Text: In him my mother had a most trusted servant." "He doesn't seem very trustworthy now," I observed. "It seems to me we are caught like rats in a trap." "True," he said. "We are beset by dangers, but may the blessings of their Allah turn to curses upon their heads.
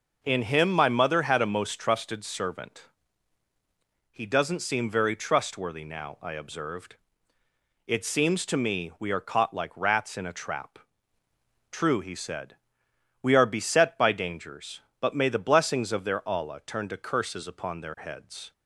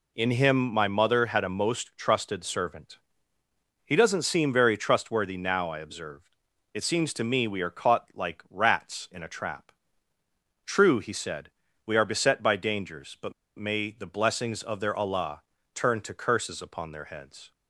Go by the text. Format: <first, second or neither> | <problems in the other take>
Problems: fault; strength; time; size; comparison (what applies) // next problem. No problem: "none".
first | pauses between "but" and "may"; slight; at 13.3 s; 0.24 s long // pauses between "Allah" and "turn"; slight; at 15.4 s; 0.32 s long